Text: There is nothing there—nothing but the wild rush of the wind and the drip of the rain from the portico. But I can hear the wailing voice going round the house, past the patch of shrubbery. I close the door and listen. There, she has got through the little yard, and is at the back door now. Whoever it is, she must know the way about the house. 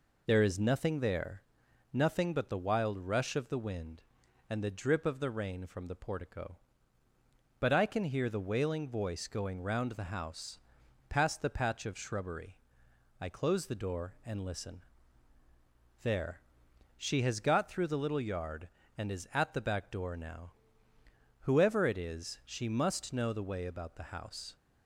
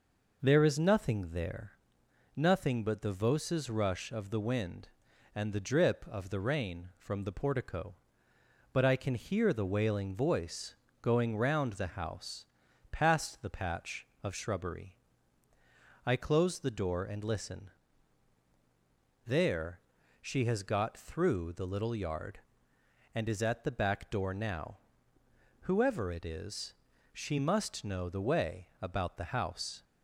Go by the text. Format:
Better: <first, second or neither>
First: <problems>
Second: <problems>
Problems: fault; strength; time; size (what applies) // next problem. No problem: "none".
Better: first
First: none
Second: says "voces" for "wild"; at 3.1 s // pauses between "voice" and "going"; slight; at 10.7 s; 0.30 s long